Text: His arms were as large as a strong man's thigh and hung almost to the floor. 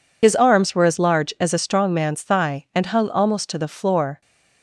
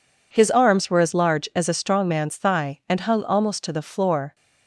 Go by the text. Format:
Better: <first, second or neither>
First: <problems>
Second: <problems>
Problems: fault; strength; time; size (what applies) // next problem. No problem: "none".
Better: second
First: loses the start of "His"; at 0.2 s; 55 ms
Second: none